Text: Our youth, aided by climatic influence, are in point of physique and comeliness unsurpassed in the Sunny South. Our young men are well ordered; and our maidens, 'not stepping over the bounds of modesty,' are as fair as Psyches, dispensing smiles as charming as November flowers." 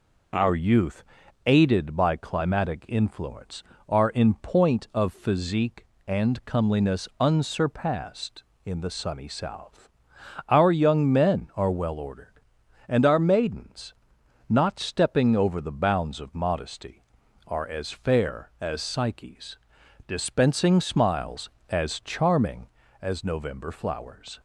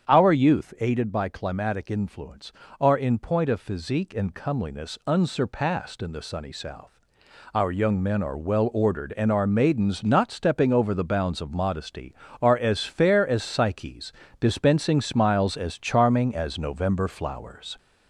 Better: first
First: none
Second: gets louder; slight; throughout; 3 dB // starts louder than the rest; strong; until 1.1 s; 8 dB

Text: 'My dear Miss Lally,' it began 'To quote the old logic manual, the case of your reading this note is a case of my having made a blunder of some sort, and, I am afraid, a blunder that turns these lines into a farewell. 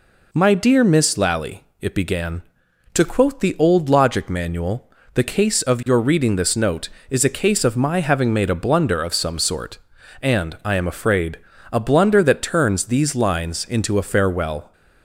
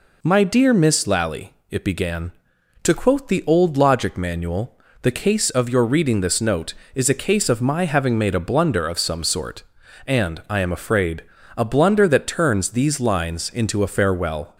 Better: neither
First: none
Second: none

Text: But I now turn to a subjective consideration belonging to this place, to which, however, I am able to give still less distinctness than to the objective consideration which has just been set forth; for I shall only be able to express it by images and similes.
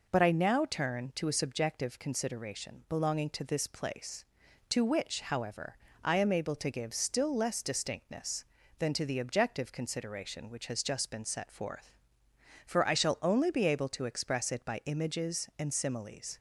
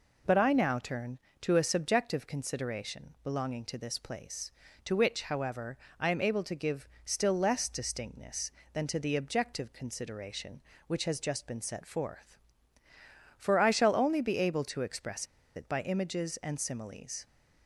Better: first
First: none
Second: pauses between "give" and "still"; slight; at 6.8 s; 0.16 s long // pauses between "express" and "it"; slight; at 15.2 s; 0.31 s long

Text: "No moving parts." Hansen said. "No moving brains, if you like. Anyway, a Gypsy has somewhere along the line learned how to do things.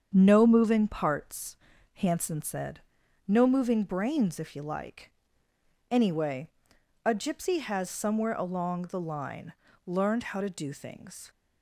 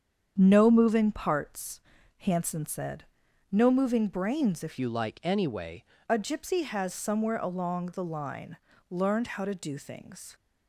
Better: first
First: starts louder than the rest; strong; until 1.1 s; 7.5 dB // pauses between "line" and "learned"; slight; at 9.5 s; 0.34 s long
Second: starts louder than the rest; strong; until 1.3 s; 7.5 dB // changes voice from "you" to "Anyway"; from 4.7 to 5.8 s; 1.1 s long // pauses between "line" and "learned"; slight; at 8.5 s; 0.34 s long

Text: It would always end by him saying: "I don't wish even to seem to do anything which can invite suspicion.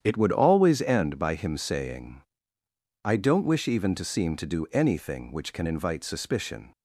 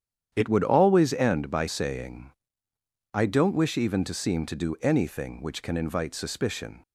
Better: first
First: starts louder than the rest; strong; until 1.0 s; 9 dB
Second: starts louder than the rest; strong; until 1.3 s; 9 dB // skips "him"; at 1.6 s

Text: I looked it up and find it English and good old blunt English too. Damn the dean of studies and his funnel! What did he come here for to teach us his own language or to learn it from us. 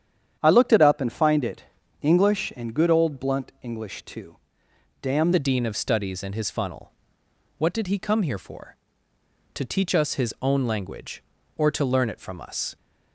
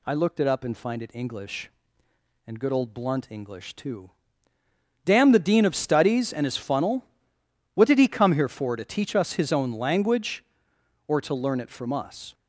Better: second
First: starts louder than the rest; strong; until 1.4 s; 9 dB // pauses between "it" and "English"; slight; at 1.6 s; 0.36 s long // changes voice at "the"; from 5.3 s on; 7.4 s long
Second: none

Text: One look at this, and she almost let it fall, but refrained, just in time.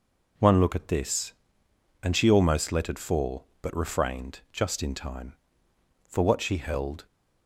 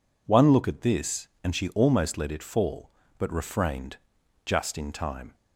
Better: second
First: goes on to say "For what she held"; noticeable; from 6.0 s on; 0.96 s long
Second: none

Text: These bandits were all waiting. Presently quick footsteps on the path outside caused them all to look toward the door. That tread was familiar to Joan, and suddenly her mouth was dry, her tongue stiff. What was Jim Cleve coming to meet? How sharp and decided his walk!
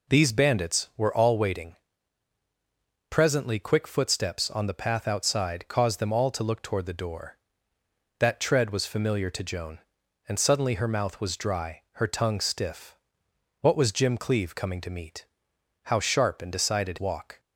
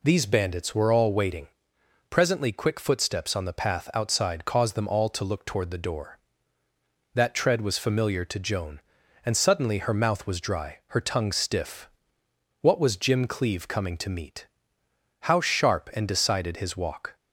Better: second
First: skips "his"; at 16.9 s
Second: none

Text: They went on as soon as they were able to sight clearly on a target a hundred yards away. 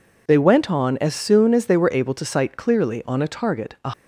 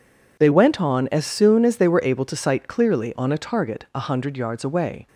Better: second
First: stops before "hundred yards away"; at 3.9 s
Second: none

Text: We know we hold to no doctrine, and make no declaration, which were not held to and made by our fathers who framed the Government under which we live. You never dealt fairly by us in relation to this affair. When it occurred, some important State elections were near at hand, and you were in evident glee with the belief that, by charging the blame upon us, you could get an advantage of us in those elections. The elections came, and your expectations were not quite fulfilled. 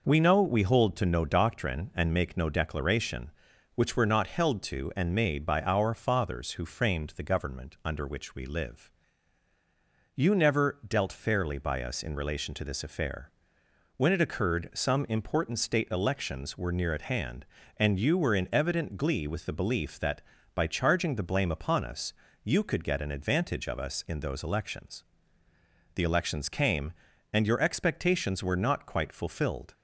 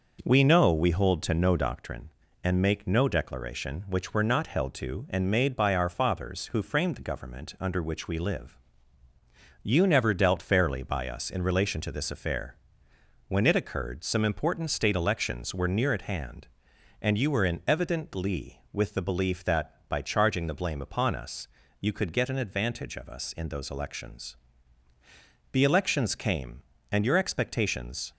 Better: first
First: none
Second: stops before "were not quite fulfilled"; at 28.1 s

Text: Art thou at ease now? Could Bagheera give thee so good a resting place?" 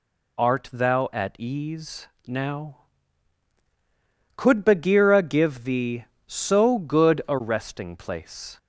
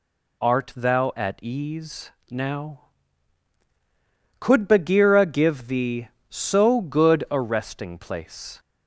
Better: neither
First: pauses between "ease" and "now"; slight; at 2.0 s; 0.18 s long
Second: pauses between "ease" and "now"; slight; at 2.1 s; 0.18 s long

